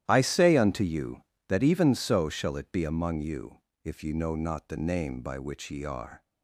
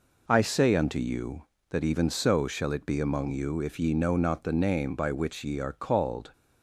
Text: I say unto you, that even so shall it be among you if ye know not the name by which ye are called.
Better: second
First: starts louder than the rest; strong; until 1.0 s; 12 dB // pauses between "you" and "if"; slight; at 3.5 s; 0.26 s long // stops before "called"; at 6.2 s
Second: none

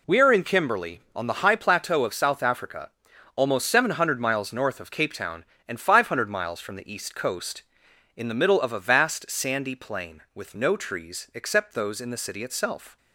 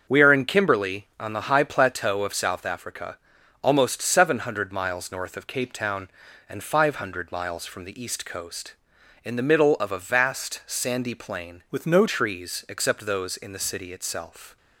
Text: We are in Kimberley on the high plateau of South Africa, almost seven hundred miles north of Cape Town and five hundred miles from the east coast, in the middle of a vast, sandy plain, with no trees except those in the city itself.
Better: first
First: none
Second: starts louder than the rest; until 1.2 s; 6.5 dB // changes voice from "with" to "no"; from 11.7 to 12.0 s; 0.3 s long

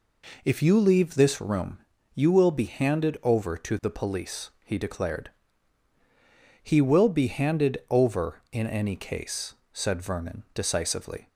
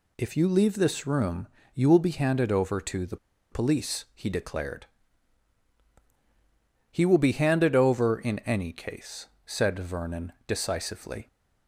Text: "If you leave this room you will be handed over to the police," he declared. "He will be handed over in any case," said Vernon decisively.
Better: first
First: pauses between "room" and "you"; slight; at 1.8 s; 0.34 s long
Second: pauses between "room" and "you"; slight; at 1.4 s; 0.26 s long // pauses between "the" and "police"; slight; at 3.1 s; 0.35 s long // pauses between "Vernon" and "decisively"; slight; at 10.3 s; 0.16 s long

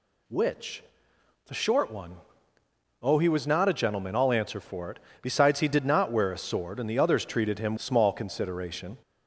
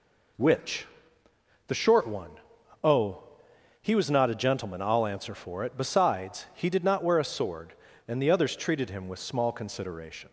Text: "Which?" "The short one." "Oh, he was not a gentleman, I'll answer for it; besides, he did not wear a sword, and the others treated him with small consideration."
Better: second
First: skips "with"; at 7.7 s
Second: none

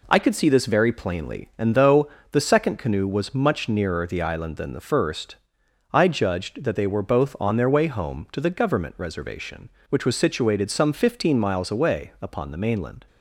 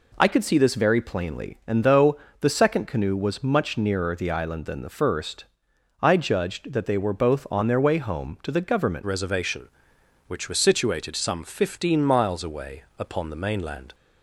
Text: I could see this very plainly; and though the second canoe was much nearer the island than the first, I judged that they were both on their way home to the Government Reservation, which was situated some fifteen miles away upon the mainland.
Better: first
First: pauses between "though" and "the"; slight; at 2.0 s; 0.24 s long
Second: pauses between "though" and "the"; slight; at 2.1 s; 0.24 s long // changes voice at "Reservation"; from 9.0 s on; 4.9 s long // pauses between "away" and "upon"; slight; at 12.8 s; 0.16 s long

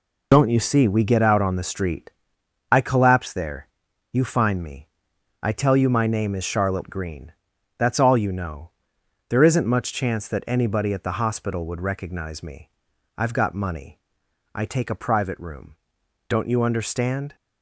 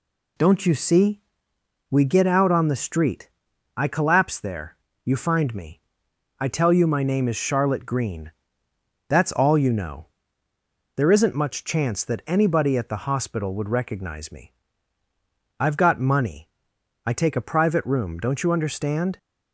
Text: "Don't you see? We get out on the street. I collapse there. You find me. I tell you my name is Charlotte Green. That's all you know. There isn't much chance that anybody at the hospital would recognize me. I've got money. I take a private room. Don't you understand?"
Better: second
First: loses the start of "Don't"; at 0.3 s; 55 ms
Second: none

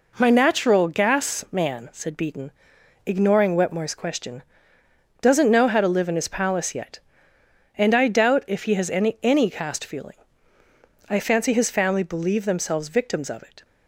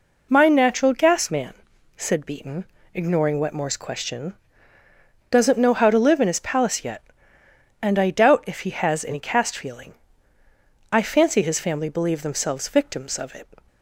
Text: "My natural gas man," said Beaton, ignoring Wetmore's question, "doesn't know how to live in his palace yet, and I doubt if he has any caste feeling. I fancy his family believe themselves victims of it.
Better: second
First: says "any" twice; at 9.2 s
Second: none

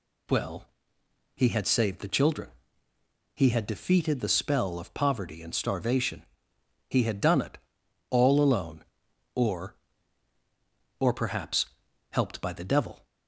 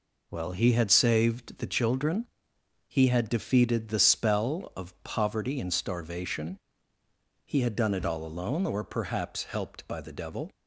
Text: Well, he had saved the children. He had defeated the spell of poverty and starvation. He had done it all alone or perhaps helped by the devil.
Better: second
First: pauses between "it" and "all"; noticeable; at 7.5 s; 0.52 s long // says "or" twice; at 10.9 s // pauses between "perhaps" and "helped"; at 11.6 s; 0.44 s long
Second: none

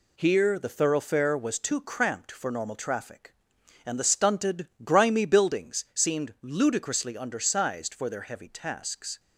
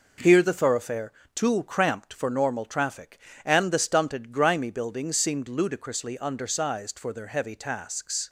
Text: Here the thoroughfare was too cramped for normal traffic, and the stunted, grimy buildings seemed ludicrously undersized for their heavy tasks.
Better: first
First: none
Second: skips "was"; at 1.2 s

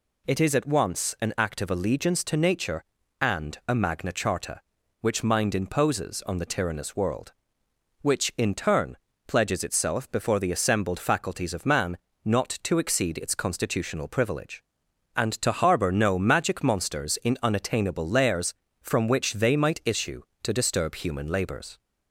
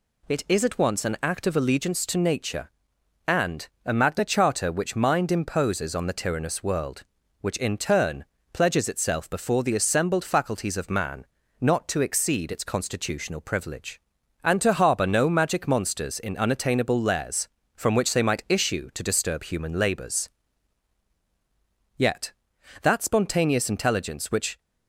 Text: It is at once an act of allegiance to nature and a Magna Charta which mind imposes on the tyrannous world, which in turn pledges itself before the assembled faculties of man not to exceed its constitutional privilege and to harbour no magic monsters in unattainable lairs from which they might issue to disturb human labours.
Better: first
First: pauses between "turn" and "pledges"; slight; at 8.9 s; 0.30 s long // pauses between "man" and "not"; slight; at 11.9 s; 0.26 s long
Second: pauses between "and" and "a"; slight; at 3.6 s; 0.18 s long // pauses between "turn" and "pledges"; slight; at 8.2 s; 0.28 s long // pauses between "man" and "not"; slight; at 11.2 s; 0.34 s long // goes on to say "Yet that spontaneous intelligence which"; strong; from 21.9 s on; 2.6 s long

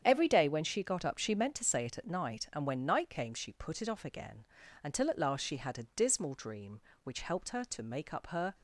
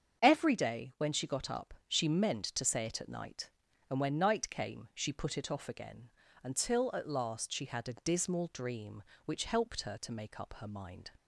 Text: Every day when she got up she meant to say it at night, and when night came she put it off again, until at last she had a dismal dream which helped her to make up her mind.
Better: second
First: starts louder than the rest; strong; until 1.0 s; 8.5 dB // stops before "mind"; at 8.5 s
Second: starts louder than the rest; strong; until 1.2 s; 7 dB

